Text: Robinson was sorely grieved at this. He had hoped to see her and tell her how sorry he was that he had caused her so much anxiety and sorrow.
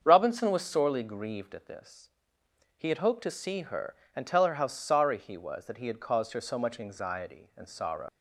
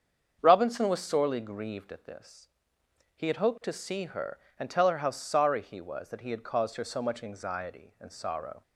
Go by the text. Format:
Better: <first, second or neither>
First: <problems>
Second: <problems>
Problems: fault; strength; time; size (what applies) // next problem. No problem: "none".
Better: second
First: starts louder than the rest; until 1.0 s; 7 dB // leaves "sorrow" unfinished; at 8.0 s; 100 ms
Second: starts louder than the rest; strong; until 1.4 s; 7 dB